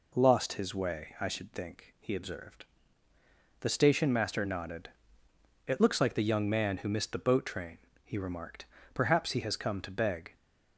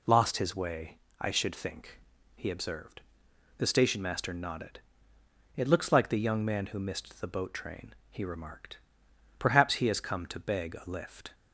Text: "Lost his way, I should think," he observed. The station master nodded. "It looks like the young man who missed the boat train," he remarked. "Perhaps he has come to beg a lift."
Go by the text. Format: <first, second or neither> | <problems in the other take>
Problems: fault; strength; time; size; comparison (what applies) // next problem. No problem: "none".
second | stops before "a lift"; at 10.3 s